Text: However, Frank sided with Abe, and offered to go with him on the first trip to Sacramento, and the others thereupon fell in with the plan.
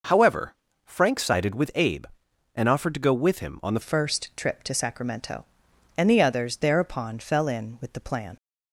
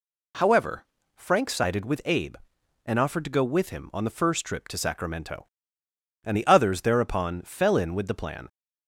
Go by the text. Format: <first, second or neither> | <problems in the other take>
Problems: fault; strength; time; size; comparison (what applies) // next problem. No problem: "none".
second | changes voice at "first"; from 3.8 s on; 4.5 s long